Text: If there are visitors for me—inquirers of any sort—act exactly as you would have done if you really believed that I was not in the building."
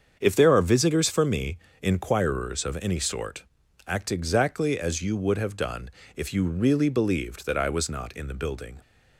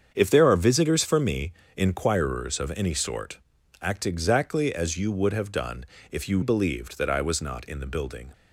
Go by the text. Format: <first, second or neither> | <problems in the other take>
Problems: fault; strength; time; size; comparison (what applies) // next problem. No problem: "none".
first | starts louder than the rest; strong; until 1.1 s; 7 dB; also in the first // pauses between "done" and "if"; slight; at 5.8 s; 0.26 s long; slight in the first // skips "really"; at 6.4 s